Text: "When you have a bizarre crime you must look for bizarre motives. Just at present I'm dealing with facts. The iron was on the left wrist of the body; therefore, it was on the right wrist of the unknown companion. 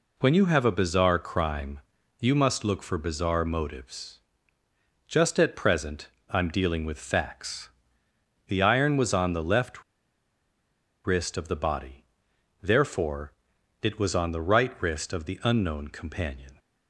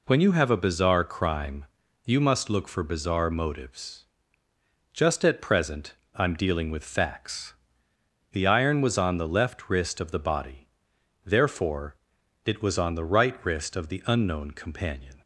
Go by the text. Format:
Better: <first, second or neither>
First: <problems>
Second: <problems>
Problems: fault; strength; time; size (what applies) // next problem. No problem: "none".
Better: second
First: pauses between "crime" and "you"; at 1.7 s; 0.40 s long // pauses between "present" and "I'm"; slight; at 6.0 s; 0.24 s long // pauses between "left" and "wrist"; at 9.8 s; 1.2 s long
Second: pauses between "crime" and "you"; at 1.6 s; 0.40 s long // pauses between "present" and "I'm"; slight; at 5.9 s; 0.24 s long